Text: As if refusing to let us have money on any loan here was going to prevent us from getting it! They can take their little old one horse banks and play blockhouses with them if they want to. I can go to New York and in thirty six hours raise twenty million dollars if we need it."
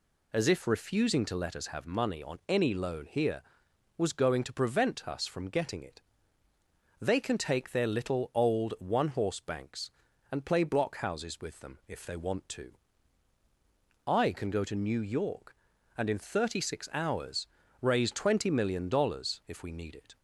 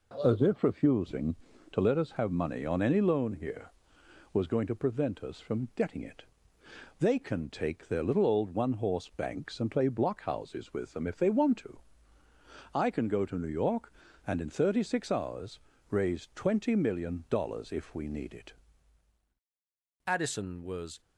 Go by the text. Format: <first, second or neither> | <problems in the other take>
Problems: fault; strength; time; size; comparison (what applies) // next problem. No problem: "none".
first | pauses between "hours" and "raise"; slight; at 15.5 s; 0.32 s long; slight in the first // goes on to say "Addison was"; noticeable; from 20.0 s on; 0.94 s long